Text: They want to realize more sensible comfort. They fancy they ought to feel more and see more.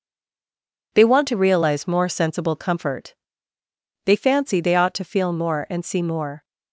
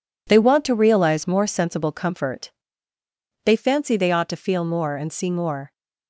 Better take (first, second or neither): second